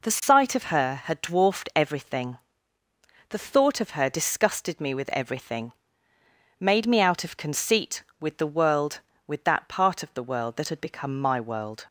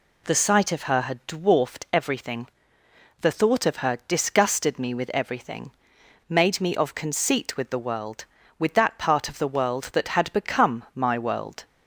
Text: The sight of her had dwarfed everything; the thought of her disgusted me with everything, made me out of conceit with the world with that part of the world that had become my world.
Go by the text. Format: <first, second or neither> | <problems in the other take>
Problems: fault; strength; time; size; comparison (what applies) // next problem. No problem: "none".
first | skips "out"; at 6.7 s